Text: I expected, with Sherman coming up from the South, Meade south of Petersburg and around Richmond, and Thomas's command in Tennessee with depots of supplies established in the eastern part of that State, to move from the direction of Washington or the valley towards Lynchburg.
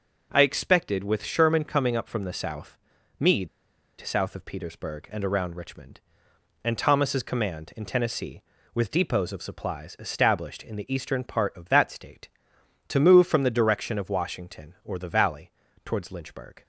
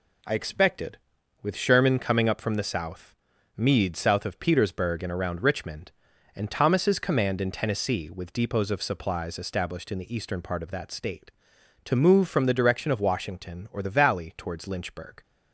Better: second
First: pauses between "Meade" and "south"; noticeable; at 3.4 s; 0.54 s long // pauses between "valley" and "towards"; slight; at 15.5 s; 0.34 s long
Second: none

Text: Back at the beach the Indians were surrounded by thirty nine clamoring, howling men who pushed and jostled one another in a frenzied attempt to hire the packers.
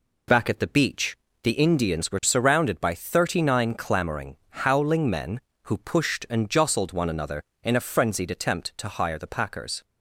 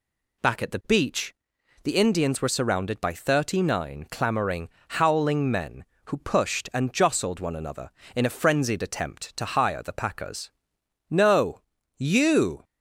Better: first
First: pauses between "beach" and "the"; slight; at 1.1 s; 0.24 s long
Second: pauses between "beach" and "the"; noticeable; at 1.3 s; 0.50 s long // goes on to say "No you"; from 11.0 s on; 1.5 s long

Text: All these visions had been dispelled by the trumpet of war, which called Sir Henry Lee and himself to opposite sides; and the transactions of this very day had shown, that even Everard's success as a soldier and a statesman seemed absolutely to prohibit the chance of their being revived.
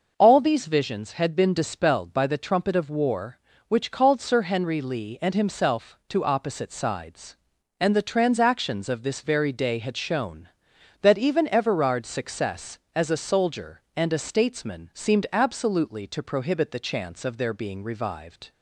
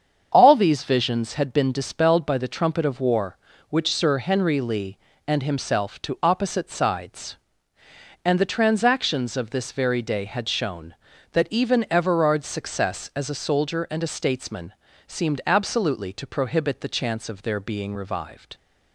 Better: first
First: none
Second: starts louder than the rest; strong; until 1.3 s; 7.5 dB // skips "called"; at 3.9 s // pauses between "statesman" and "seemed"; slight; at 14.7 s; 0.34 s long

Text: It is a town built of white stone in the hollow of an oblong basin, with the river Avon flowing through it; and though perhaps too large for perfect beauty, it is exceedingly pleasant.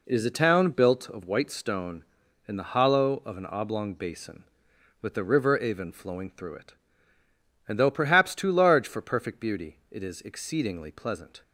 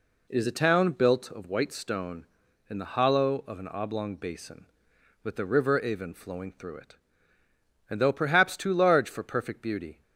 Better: first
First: none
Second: stops before "it is exceedingly pleasant"; at 10.0 s

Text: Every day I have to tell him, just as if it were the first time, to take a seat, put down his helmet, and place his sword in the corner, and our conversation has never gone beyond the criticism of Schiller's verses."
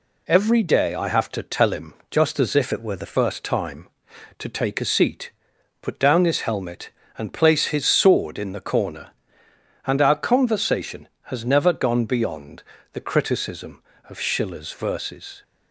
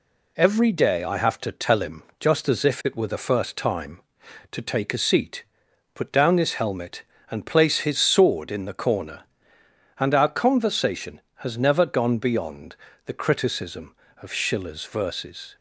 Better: second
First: changes voice from "it" to "the"; from 2.7 to 3.1 s; 0.4 s long // pauses between "beyond" and "the"; slight; at 12.6 s; 0.30 s long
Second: pauses between "beyond" and "the"; slight; at 12.7 s; 0.30 s long

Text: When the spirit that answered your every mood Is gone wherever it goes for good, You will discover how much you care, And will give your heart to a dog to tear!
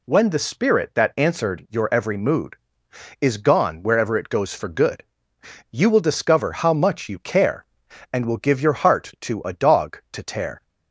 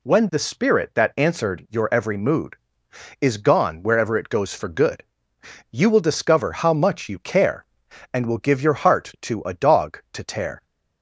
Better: neither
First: none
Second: none

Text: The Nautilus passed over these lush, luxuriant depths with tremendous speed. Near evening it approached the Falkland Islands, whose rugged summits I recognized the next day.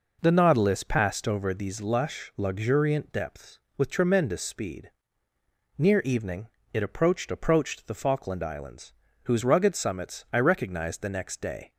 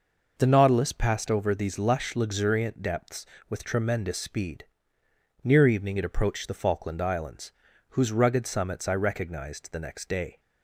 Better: second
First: pauses between "evening" and "it"; slight; at 6.4 s; 0.26 s long // says "approached" twice; at 7.3 s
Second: none

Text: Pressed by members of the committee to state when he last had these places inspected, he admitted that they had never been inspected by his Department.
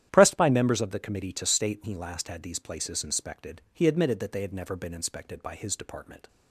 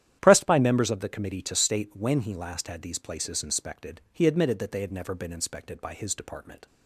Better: second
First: starts louder than the rest; strong; until 1.1 s; 11 dB // skips "when"; at 1.8 s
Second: starts louder than the rest; strong; until 1.2 s; 11 dB

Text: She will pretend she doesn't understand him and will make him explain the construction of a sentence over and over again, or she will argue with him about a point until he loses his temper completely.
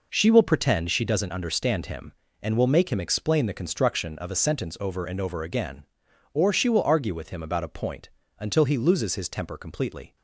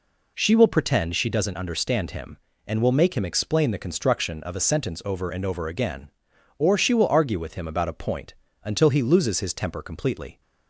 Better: second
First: gets quieter; strong; throughout; 9 dB // pauses between "point" and "until"; slight; at 8.0 s; 0.30 s long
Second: pauses between "point" and "until"; slight; at 8.3 s; 0.30 s long

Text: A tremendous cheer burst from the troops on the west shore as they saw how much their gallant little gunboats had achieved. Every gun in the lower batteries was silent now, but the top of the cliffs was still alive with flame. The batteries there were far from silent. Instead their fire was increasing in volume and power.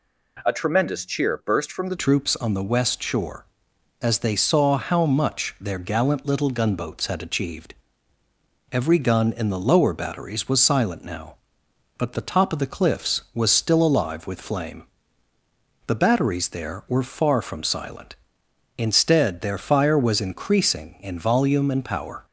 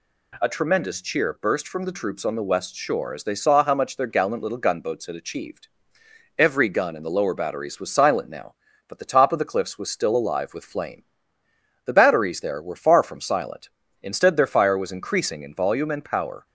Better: second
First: changes voice at "troops"; from 1.9 s on; 20.3 s long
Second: none

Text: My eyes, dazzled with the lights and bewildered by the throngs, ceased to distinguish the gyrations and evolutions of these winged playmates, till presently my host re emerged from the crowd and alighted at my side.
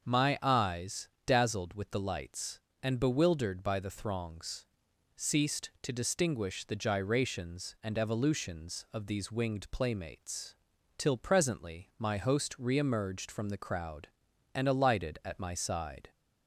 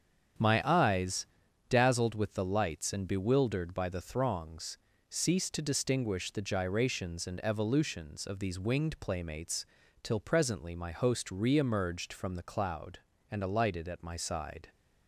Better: first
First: starts louder than the rest; until 1.0 s; 6.5 dB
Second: starts louder than the rest; strong; until 1.8 s; 8 dB // says "cloud" for "crowd"; at 12.4 s

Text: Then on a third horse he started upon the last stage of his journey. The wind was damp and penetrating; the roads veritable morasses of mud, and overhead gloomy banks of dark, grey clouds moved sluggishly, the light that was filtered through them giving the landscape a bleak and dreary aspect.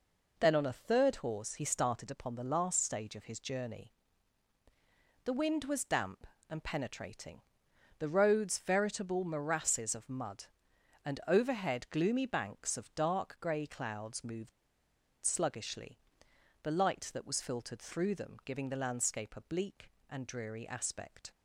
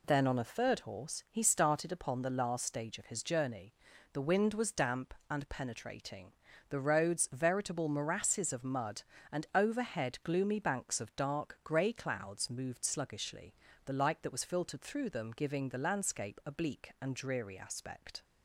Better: second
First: pauses between "moved" and "sluggishly"; noticeable; at 14.5 s; 0.71 s long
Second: none

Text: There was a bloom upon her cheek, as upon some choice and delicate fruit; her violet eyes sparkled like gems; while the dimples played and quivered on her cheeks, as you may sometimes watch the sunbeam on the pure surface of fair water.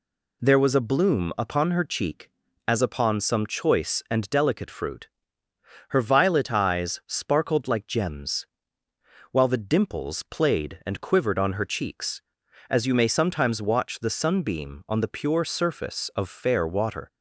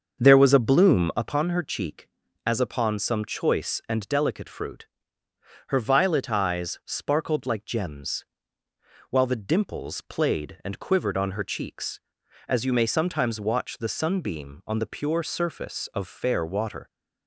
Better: first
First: none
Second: starts louder than the rest; until 1.4 s; 6.5 dB

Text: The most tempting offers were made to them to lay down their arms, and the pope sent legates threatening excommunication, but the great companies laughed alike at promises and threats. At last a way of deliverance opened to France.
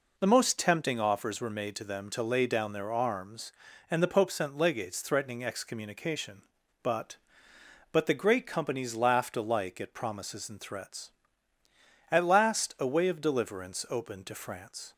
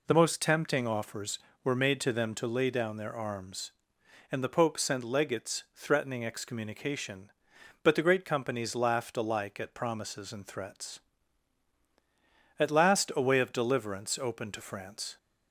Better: second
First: says "but" twice; at 7.9 s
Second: none

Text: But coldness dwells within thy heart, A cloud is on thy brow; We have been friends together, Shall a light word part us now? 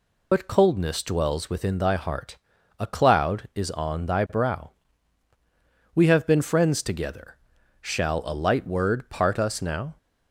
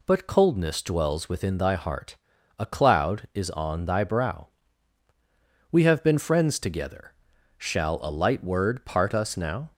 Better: second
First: loses the start of "But"; at 0.3 s; 105 ms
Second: none

